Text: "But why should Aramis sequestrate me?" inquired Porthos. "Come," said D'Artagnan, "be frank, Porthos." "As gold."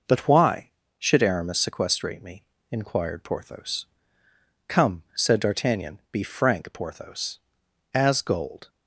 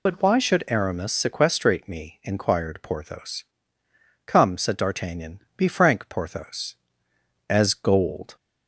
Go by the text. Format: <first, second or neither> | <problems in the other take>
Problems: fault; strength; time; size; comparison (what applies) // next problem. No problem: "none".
first | loses the start of "But"; at 0.0 s; 65 ms